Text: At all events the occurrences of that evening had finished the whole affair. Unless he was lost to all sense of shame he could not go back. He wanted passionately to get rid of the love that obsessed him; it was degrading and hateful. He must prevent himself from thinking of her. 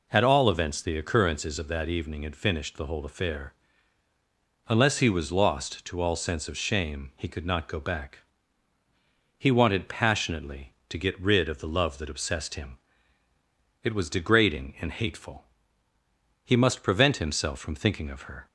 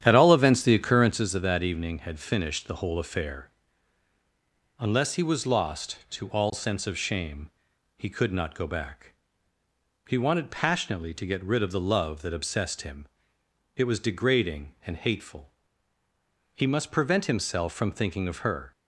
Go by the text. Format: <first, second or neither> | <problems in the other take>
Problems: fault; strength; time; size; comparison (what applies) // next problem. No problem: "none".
first | starts louder than the rest; strong; until 1.3 s; 10 dB // pauses between "shame" and "he"; noticeable; at 7.4 s; 0.46 s long